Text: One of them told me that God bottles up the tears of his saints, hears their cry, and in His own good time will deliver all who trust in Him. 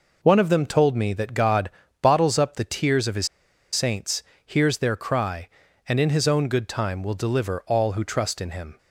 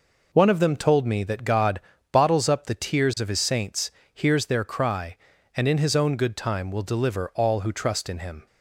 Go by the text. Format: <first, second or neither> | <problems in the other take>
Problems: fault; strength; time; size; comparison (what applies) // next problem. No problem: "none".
second | pauses between "God" and "bottles"; slight; at 1.6 s; 0.32 s long; slight in the second // pauses between "his" and "saints"; noticeable; at 3.2 s; 0.46 s long